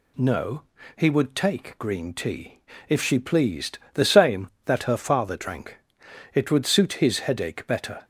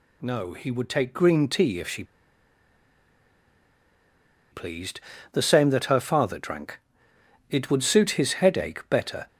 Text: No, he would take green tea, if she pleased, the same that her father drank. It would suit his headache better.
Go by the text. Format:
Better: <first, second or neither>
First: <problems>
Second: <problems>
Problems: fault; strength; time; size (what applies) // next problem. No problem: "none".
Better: first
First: none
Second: pauses between "she" and "pleased"; strong; at 2.0 s; 2.4 s long